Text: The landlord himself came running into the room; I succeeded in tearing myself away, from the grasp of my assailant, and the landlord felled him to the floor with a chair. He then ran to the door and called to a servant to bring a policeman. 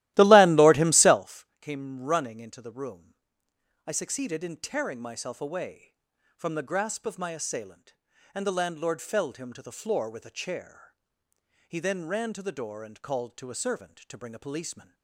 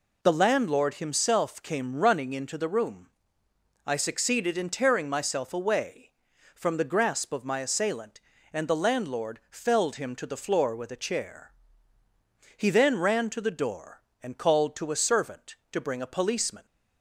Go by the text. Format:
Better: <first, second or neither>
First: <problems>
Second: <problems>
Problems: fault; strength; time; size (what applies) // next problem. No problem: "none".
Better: second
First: starts louder than the rest; strong; until 1.3 s; 16 dB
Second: none